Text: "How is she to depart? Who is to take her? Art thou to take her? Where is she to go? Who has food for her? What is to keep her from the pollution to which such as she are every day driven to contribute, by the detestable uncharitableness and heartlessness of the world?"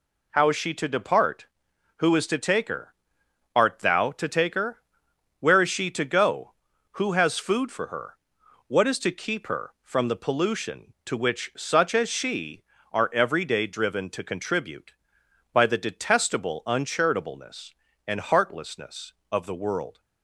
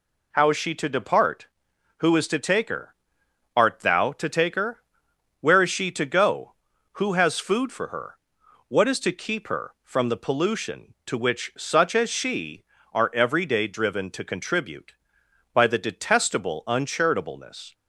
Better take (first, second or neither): first